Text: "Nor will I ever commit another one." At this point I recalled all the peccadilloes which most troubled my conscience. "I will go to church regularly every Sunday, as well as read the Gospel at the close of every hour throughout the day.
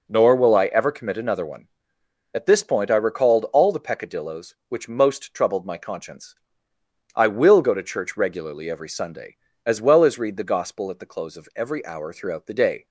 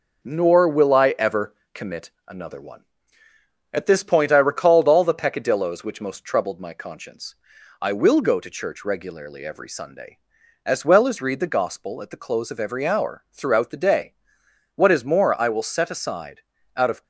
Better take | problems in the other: first | pauses between "ever" and "commit"; slight; at 1.5 s; 0.20 s long // pauses between "commit" and "another"; slight; at 2.1 s; 0.16 s long // goes on to say "What is more I will set aside out of"; strong; from 14.7 s on; 2.2 s long

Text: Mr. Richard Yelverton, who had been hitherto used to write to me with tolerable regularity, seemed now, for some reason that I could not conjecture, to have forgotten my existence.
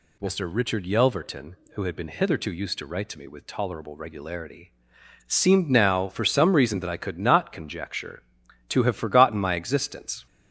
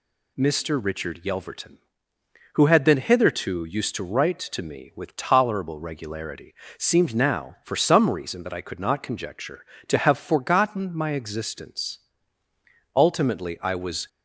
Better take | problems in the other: first | goes on to say "Ultimately I was"; noticeable; from 12.9 s on; 1.1 s long

